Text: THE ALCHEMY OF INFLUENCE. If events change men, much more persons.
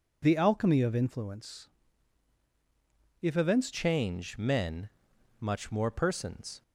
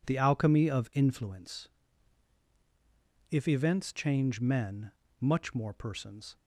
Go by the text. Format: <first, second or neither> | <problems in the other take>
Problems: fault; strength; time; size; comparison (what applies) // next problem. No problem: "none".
second | changes voice at "change"; from 3.7 s on; 2.9 s long